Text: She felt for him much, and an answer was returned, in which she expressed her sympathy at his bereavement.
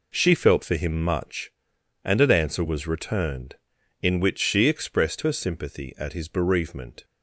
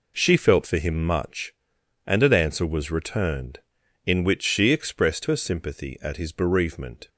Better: neither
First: none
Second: none

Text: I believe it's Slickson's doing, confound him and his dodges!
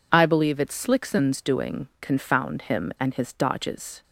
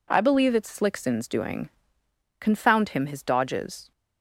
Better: first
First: none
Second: skips "and"; at 3.0 s

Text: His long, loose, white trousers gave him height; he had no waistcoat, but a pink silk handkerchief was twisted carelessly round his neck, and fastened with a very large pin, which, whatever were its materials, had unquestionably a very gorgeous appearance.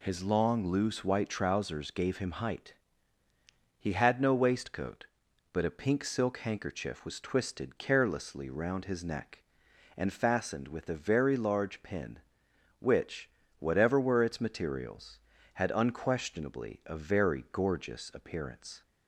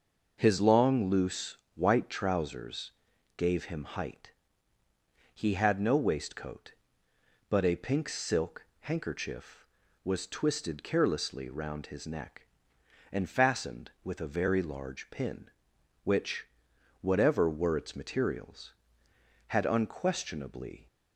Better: first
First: none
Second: pauses between "trousers" and "gave"; at 2.9 s; 0.42 s long // pauses between "silk" and "handkerchief"; slight; at 8.6 s; 0.18 s long // stops before "a very gorgeous appearance"; at 20.8 s

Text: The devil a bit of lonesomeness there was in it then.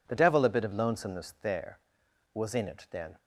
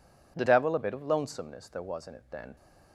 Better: neither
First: none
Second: none

